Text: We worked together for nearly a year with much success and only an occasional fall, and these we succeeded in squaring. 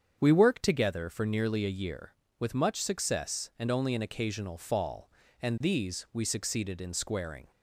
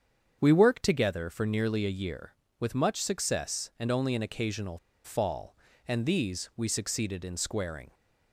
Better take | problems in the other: first | starts louder than the rest; strong; until 1.4 s; 7.5 dB; strong in the first // pauses between "occasional" and "fall"; slight; at 4.7 s; 0.26 s long

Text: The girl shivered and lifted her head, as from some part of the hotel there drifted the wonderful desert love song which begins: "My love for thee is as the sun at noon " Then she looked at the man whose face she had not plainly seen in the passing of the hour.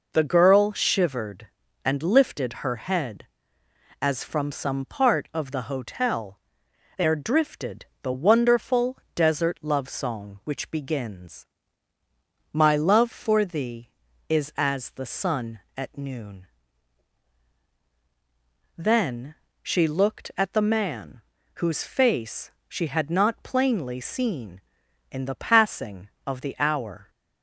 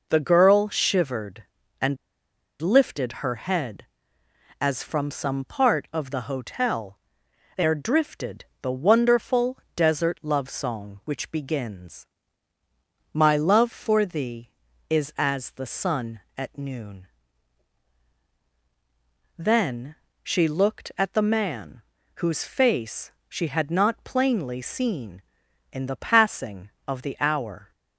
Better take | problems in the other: first | pauses between "and" and "lifted"; noticeable; at 1.9 s; 0.64 s long // pauses between "hotel" and "there"; noticeable; at 6.9 s; 0.58 s long; noticeable in the first // pauses between "drifted" and "the"; slight; at 8.4 s; 0.16 s long; slight in the first // pauses between "wonderful" and "desert"; slight; at 9.5 s; 0.18 s long; slight in the first // pauses between "Then" and "she"; slight; at 19.9 s; 0.28 s long; slight in the first // pauses between "man" and "whose"; slight; at 21.8 s; 0.36 s long; slight in the first // pauses between "face" and "she"; slight; at 23.1 s; 0.16 s long; slight in the first

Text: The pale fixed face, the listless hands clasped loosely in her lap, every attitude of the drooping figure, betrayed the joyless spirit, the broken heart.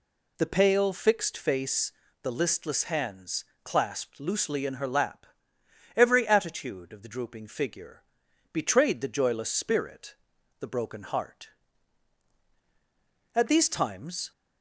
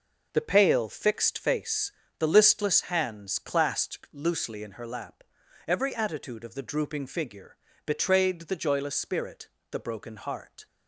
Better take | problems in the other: second | pauses between "hands" and "clasped"; slight; at 3.4 s; 0.18 s long // goes on to say "At these times"; noticeable; from 13.3 s on; 0.98 s long

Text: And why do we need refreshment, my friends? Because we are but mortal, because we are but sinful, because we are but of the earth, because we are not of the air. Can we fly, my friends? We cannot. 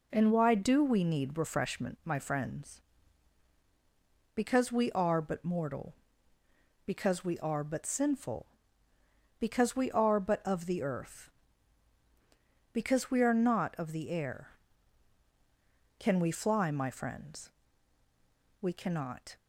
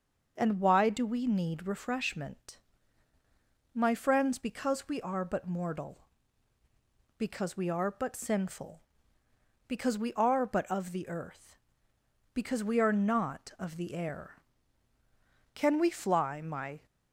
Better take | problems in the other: first | starts louder than the rest; until 1.3 s; 6 dB // stops before "friends We cannot"; at 16.8 s

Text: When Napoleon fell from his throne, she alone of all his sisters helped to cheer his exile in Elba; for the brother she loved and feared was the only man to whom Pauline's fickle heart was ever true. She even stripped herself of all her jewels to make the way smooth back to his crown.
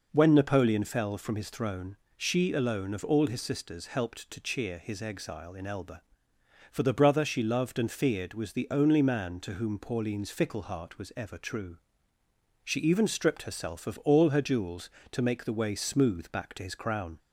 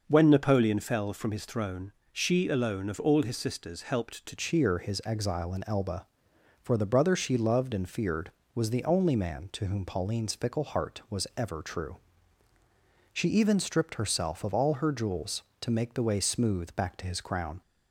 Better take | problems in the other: first | changes voice at "cheer"; from 4.3 s on; 13.3 s long

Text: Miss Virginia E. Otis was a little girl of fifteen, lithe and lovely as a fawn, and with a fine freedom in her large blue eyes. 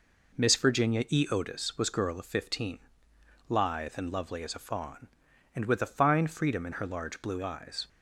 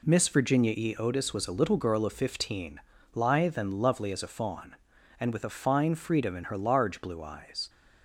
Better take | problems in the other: second | skips "a little"; at 1.9 s

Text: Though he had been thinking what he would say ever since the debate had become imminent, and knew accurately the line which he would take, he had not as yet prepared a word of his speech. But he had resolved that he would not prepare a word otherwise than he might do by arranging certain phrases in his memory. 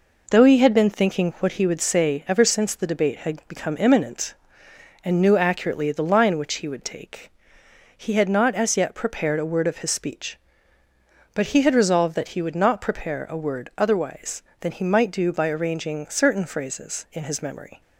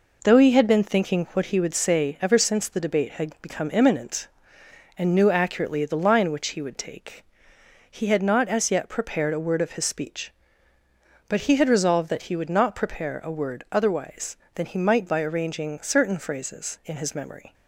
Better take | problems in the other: first | skips "do"; at 15.0 s

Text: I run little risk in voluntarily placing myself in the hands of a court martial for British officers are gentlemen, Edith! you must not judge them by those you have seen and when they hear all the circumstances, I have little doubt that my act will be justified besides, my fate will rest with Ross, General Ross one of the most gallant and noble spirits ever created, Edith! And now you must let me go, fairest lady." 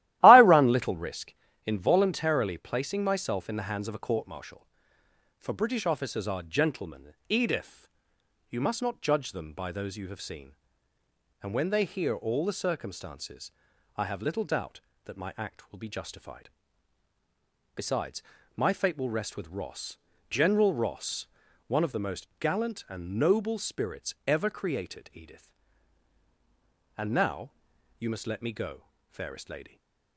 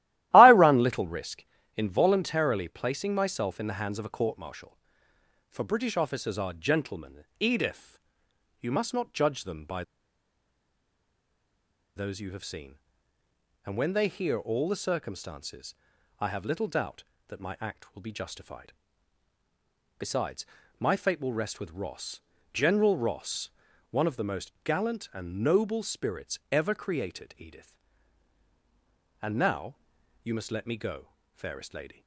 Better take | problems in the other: first | starts louder than the rest; strong; until 1.3 s; 15 dB; strong in the first // pauses between "by" and "those"; strong; at 9.8 s; 2.1 s long // pauses between "justified" and "besides"; at 18.7 s; 1.2 s long; also in the first // pauses between "Ross" and "one"; at 23.5 s; 0.40 s long; also in the first // pauses between "now" and "you"; noticeable; at 29.7 s; 0.48 s long; noticeable in the first

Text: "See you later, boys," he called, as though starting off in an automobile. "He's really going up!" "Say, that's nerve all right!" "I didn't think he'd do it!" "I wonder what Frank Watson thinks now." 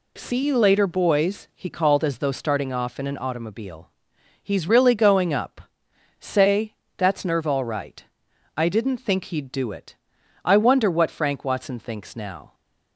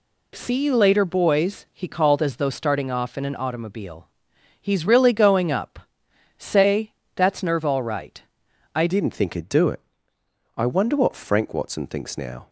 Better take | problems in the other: first | changes voice at "didn't"; from 8.8 s on; 3.6 s long

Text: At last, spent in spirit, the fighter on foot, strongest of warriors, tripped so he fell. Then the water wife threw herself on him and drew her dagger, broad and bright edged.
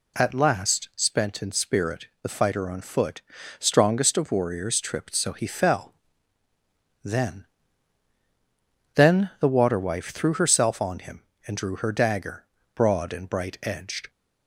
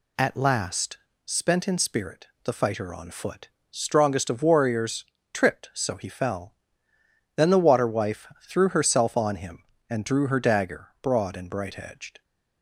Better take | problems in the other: second | says "Then" twice; at 8.9 s

